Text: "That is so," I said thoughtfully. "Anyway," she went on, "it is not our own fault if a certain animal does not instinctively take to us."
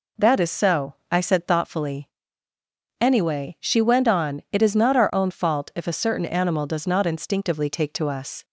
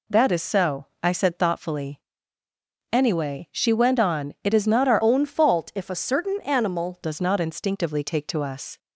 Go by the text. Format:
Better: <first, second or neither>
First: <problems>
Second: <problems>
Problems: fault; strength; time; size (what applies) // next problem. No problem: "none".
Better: first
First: none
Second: changes voice from "own" to "animal"; from 5.0 to 6.9 s; 1.9 s long